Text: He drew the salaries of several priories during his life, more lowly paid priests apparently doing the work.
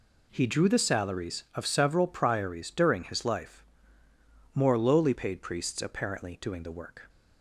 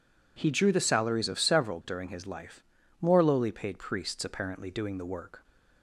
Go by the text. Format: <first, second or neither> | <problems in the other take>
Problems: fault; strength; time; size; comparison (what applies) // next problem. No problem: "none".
first | skips "priories"; at 1.8 s